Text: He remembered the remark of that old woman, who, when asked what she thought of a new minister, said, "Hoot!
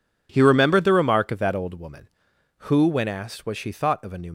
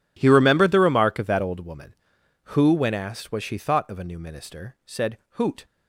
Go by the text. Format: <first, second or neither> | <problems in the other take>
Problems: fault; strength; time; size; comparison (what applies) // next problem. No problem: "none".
second | stops before "minister said Hoot"; at 4.2 s